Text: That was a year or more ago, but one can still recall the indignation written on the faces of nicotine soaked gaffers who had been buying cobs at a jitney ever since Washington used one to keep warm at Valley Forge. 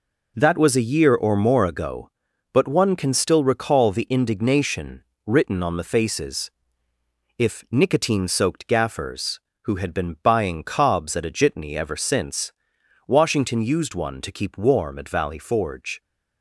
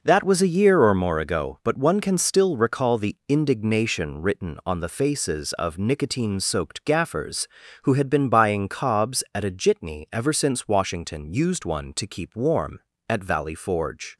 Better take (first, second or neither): second